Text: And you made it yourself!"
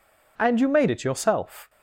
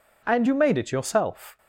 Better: neither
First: none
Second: none

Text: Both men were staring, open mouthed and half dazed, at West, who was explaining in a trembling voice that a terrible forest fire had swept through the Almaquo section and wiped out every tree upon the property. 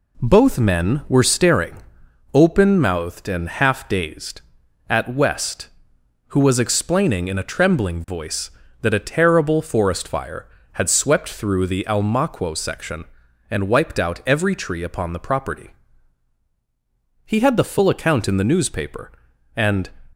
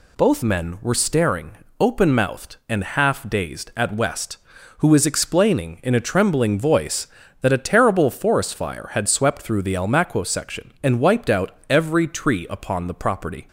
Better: second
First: goes on to say "He had the full account in the newspaper and"; strong; from 17.2 s on; 2.6 s long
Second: none

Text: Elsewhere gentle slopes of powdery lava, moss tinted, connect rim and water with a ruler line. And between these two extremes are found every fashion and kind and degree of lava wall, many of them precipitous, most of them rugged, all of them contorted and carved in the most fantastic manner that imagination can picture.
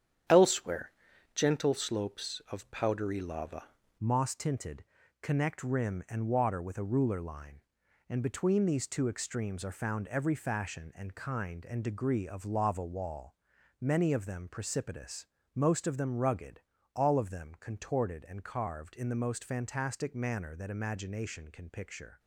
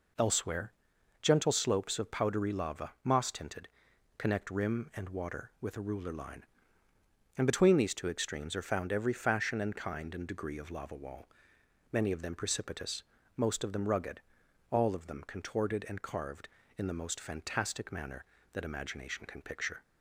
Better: second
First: starts louder than the rest; strong; until 1.7 s; 9 dB // pauses between "Elsewhere" and "gentle"; at 0.9 s; 0.44 s long // changes voice at "moss"; from 3.9 s on; 18.2 s long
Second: pauses between "Elsewhere" and "gentle"; noticeable; at 0.7 s; 0.50 s long

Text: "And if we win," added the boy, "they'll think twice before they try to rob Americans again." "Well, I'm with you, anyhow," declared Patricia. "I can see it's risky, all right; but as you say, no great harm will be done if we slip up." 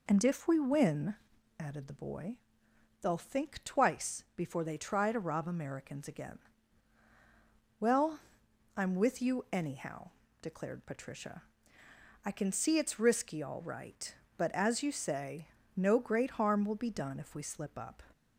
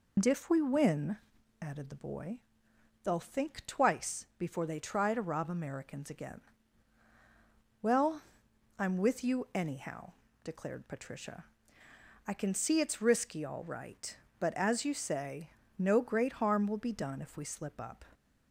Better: first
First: none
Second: loses the start of "And"; at 0.1 s; 70 ms

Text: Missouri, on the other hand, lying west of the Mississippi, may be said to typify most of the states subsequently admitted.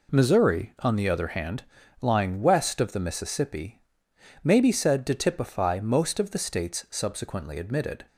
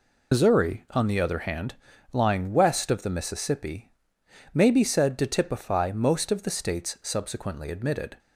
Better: first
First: none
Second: loses the start of "Missouri"; at 0.3 s; 110 ms

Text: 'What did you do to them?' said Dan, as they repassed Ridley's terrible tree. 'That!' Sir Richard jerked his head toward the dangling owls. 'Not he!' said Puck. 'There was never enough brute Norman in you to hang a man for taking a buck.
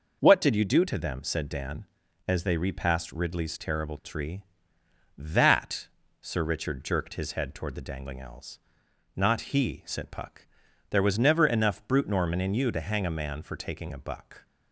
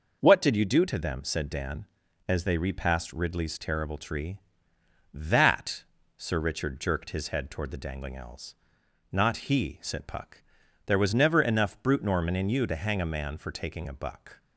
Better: neither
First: none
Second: none

